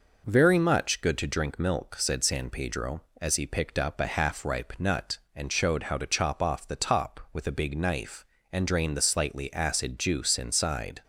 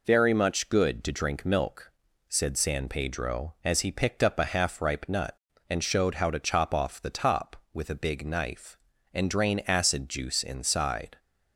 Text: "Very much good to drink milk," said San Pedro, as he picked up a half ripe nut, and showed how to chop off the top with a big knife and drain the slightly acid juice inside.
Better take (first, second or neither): first